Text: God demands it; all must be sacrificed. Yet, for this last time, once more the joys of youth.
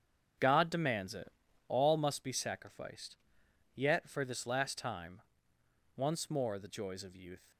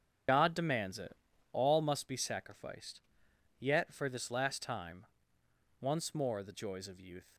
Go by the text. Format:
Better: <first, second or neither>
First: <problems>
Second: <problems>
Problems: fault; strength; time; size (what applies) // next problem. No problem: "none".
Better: first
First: starts louder than the rest; strong; until 1.7 s; 7.5 dB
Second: loses the start of "God"; at 0.2 s; 55 ms // starts louder than the rest; strong; until 1.6 s; 7.5 dB